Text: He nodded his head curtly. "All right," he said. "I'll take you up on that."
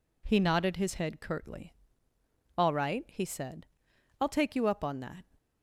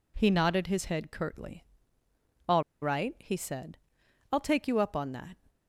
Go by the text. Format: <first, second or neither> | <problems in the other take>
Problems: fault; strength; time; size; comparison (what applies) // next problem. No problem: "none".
first | pauses between "All" and "right"; slight; at 2.6 s; 0.19 s long